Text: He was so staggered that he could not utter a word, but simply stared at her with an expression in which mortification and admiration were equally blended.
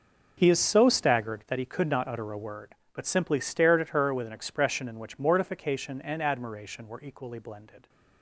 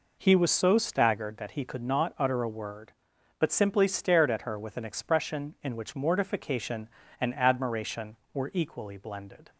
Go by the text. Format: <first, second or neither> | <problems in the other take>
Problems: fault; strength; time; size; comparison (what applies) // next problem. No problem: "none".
second | says "is" for "was"; at 0.4 s